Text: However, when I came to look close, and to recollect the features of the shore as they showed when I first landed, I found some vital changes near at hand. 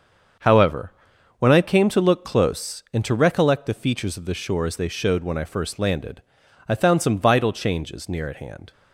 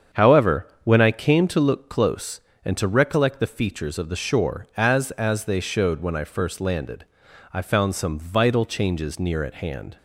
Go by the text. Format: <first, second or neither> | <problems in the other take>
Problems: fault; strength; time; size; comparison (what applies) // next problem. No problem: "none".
first | starts louder than the rest; strong; until 1.2 s; 7.5 dB; also in the first // says "as" twice; at 5.1 s